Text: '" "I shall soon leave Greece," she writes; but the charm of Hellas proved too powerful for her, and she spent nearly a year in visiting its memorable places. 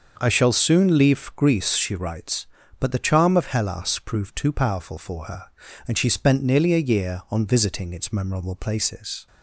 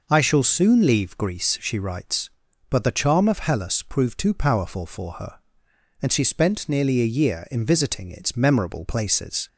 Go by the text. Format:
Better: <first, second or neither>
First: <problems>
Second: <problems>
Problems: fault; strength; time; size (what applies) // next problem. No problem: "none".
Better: second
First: starts louder than the rest; until 1.1 s; 6.5 dB // says "on" for "in"; at 7.3 s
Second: none